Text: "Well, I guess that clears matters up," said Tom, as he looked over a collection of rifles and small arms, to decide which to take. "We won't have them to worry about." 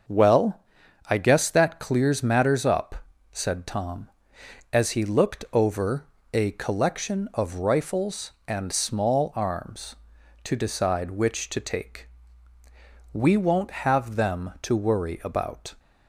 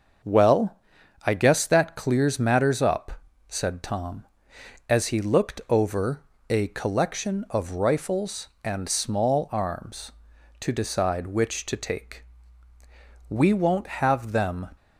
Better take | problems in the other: first | starts louder than the rest; until 1.7 s; 6.5 dB; also in the first // pauses between "over" and "a"; slight; at 6.2 s; 0.28 s long; slight in the first // stops before "to worry about"; at 14.7 s

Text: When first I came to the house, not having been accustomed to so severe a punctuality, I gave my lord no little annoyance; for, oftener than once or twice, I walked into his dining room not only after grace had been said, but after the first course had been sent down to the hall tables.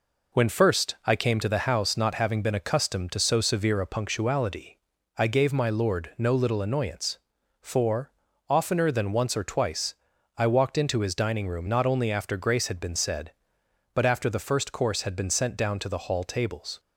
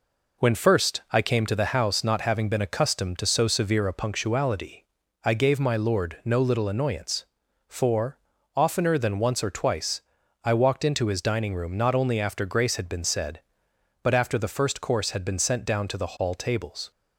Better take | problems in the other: neither | none

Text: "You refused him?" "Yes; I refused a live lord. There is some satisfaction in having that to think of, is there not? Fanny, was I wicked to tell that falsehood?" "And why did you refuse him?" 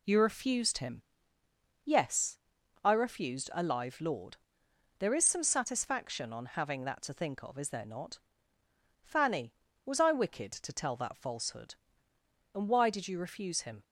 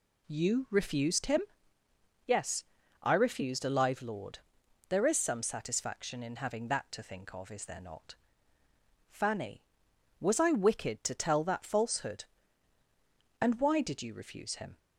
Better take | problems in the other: second | says "on" for "in"; at 6.3 s

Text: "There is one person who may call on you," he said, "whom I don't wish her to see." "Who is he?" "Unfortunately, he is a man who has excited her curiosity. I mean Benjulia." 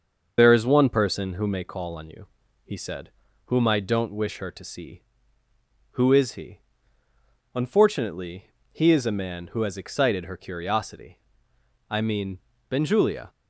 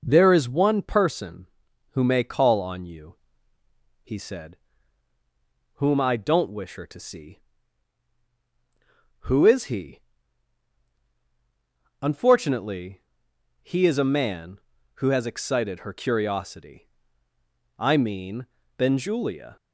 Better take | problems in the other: second | loses the start of "There"; at 0.3 s; 70 ms // starts louder than the rest; until 1.3 s; 6.5 dB // pauses between "mean" and "Benjulia"; slight; at 12.3 s; 0.30 s long; slight in the second

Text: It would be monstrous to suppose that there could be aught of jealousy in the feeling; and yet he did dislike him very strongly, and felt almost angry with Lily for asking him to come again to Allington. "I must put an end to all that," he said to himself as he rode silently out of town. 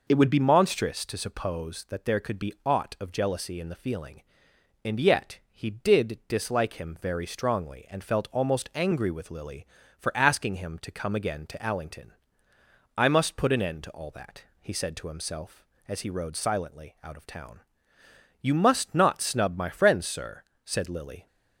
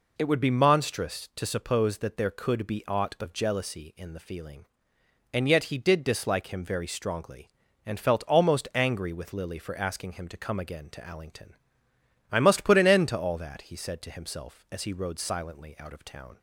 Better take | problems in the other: second | goes on to say "You must not snub my friends sir said Lily"; strong; from 18.3 s on; 2.8 s long

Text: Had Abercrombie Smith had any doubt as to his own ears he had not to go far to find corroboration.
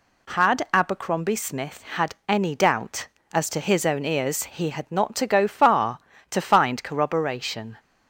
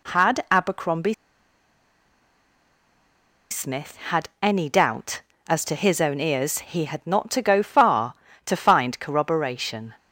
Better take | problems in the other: first | pauses between "Abercrombie" and "Smith"; strong; at 1.1 s; 2.3 s long

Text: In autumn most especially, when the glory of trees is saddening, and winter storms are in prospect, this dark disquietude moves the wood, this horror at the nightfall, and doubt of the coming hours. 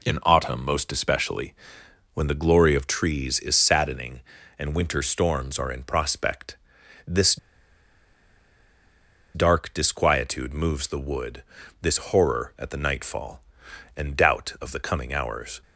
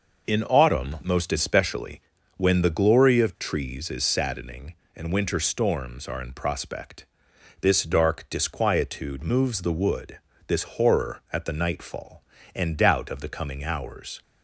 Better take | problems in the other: second | pauses between "this" and "dark"; strong; at 7.3 s; 1.9 s long

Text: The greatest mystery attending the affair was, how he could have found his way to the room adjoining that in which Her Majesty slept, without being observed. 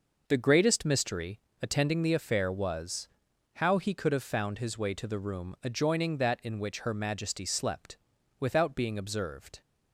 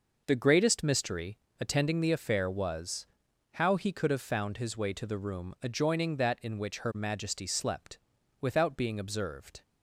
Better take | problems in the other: neither | pauses between "mystery" and "attending"; slight; the same in both

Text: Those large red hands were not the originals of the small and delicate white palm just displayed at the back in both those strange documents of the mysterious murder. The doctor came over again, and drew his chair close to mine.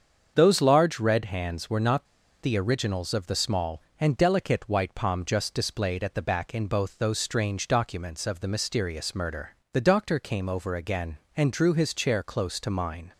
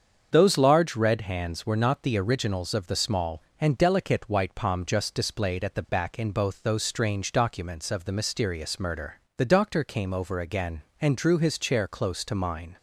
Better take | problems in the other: second | starts louder than the rest; until 1.3 s; 7 dB; also in the second // pauses between "not" and "the"; slight; at 2.0 s; 0.36 s long

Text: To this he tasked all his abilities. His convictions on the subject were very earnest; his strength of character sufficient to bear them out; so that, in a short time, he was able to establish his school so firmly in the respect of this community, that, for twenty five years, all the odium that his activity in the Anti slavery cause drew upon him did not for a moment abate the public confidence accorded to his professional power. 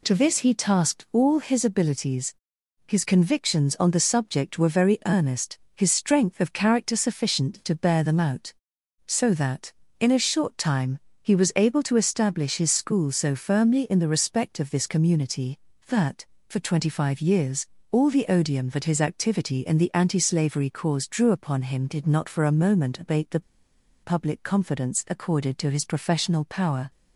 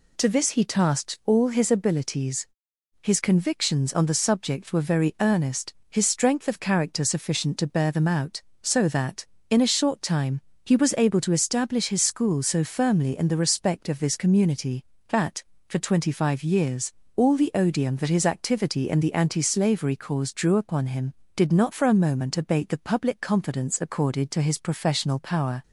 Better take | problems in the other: second | pauses between "the" and "public"; noticeable; at 23.3 s; 0.63 s long

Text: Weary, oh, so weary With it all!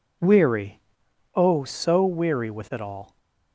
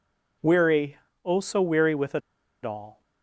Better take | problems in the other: first | pauses between "it" and "all"; at 2.2 s; 0.43 s long

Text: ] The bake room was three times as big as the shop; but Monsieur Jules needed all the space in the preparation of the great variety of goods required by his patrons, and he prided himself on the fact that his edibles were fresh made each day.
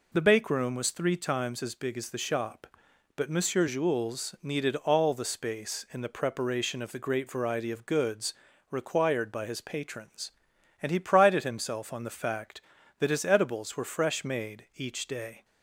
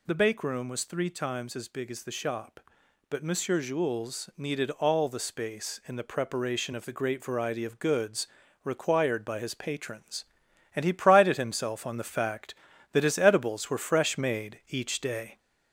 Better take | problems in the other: first | gets louder; slight; throughout; 3 dB // pauses between "goods" and "required"; at 8.2 s; 0.38 s long; also in the first

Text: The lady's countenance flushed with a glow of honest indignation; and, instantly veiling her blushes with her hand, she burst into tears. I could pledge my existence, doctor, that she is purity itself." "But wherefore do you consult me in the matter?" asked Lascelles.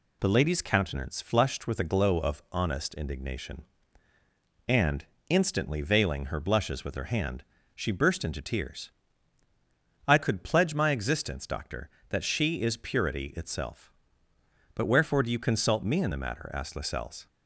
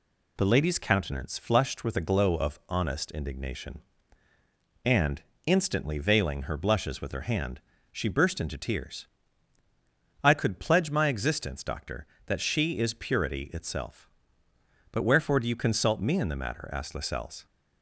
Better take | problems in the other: neither | none

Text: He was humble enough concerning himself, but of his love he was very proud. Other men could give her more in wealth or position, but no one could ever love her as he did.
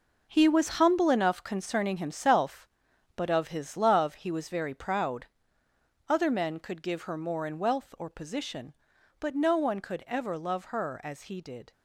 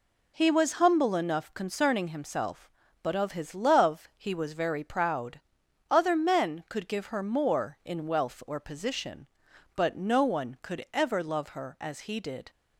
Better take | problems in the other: second | gets quieter; strong; throughout; 9.5 dB

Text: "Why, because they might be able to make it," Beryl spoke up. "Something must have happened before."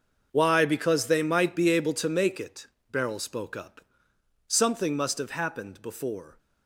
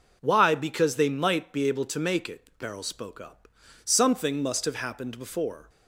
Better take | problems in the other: second | gets quieter; strong; throughout; 15 dB

